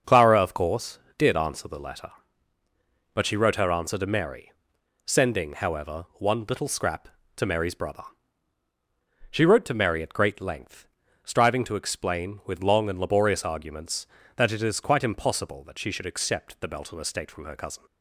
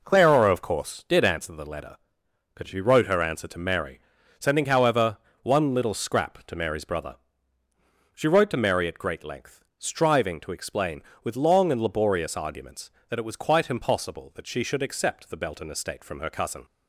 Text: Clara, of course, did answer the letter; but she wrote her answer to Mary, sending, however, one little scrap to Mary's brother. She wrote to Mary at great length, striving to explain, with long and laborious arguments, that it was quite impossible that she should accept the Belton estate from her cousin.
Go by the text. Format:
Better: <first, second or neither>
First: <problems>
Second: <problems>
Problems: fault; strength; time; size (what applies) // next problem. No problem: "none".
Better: second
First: starts louder than the rest; until 1.2 s; 6.5 dB // says "is" for "was"; at 14.6 s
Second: none